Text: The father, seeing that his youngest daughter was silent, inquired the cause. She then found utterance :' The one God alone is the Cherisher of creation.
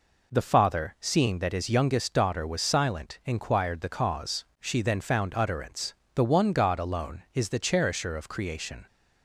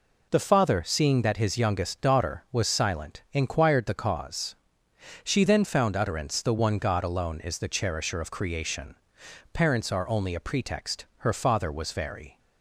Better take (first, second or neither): first